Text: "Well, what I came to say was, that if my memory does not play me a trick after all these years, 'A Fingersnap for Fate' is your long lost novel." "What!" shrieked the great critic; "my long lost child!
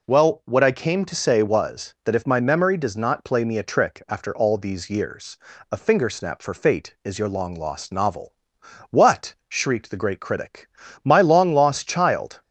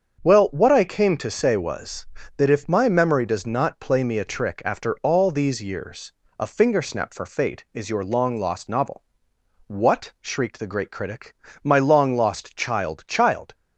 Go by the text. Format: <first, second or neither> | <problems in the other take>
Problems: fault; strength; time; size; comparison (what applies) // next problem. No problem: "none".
first | starts louder than the rest; until 1.2 s; 7 dB // says "child" twice; at 13.0 s